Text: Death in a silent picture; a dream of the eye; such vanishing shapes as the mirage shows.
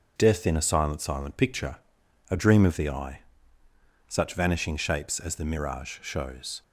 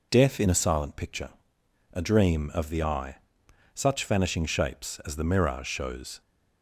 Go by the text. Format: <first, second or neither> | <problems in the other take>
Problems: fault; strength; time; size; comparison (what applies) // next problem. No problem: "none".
second | starts louder than the rest; until 1.1 s; 6.5 dB // says "silent" twice; at 0.9 s